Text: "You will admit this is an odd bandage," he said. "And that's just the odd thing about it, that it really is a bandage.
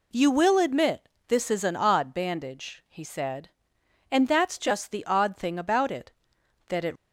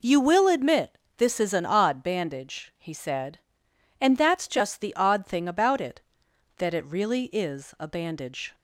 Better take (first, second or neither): second